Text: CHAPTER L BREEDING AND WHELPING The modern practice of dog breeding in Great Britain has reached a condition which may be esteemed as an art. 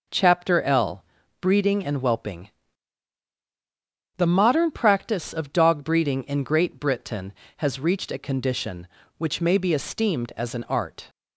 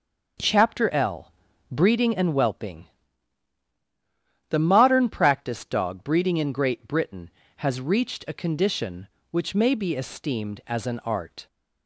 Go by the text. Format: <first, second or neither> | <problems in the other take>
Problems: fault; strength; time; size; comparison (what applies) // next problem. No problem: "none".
first | starts louder than the rest; until 1.7 s; 6.5 dB // pauses between "L" and "BREEDING"; at 1.3 s; 0.38 s long; also in the first // pauses between "WHELPING" and "The"; strong; at 2.8 s; 1.6 s long; strong in the first // skips "of"; at 5.6 s